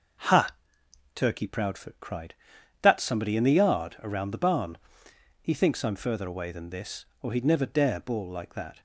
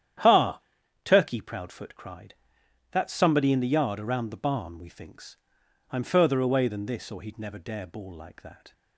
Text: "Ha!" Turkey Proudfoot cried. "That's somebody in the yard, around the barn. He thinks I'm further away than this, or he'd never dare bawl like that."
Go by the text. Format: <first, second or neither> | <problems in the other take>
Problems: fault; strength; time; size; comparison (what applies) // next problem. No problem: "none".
first | starts louder than the rest; strong; until 1.6 s; 10 dB // says "We" for "He"; at 4.7 s // pauses between "thinks" and "I'm"; noticeable; at 5.3 s; 0.56 s long